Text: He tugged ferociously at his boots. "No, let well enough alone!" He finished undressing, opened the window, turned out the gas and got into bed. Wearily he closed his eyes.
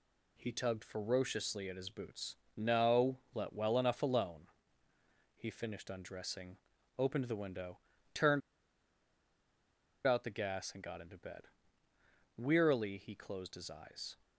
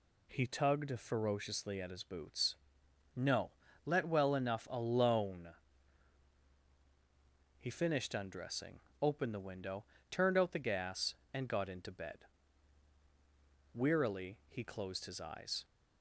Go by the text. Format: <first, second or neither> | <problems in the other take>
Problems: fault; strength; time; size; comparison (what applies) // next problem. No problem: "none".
second | pauses between "turned" and "out"; strong; at 8.4 s; 1.6 s long